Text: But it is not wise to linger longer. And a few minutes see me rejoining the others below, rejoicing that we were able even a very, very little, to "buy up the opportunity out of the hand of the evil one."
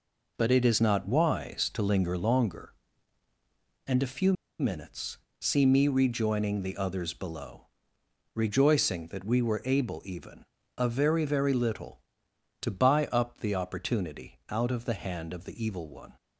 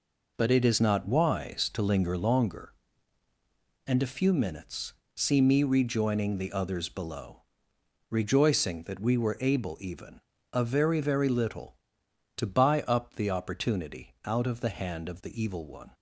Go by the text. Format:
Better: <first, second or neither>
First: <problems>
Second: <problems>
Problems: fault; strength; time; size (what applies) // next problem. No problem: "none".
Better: second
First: pauses between "few" and "minutes"; slight; at 4.3 s; 0.26 s long // pauses between "minutes" and "see"; slight; at 5.1 s; 0.22 s long // pauses between "even" and "a"; slight; at 10.4 s; 0.34 s long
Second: pauses between "minutes" and "see"; slight; at 4.9 s; 0.22 s long // pauses between "even" and "a"; slight; at 10.1 s; 0.34 s long